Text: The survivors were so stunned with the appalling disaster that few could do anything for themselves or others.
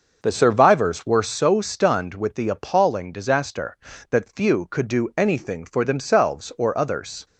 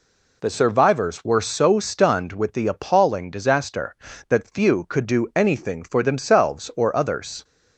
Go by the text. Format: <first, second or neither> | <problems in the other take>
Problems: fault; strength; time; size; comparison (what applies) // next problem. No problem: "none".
second | starts louder than the rest; noticeable; until 1.3 s; 6 dB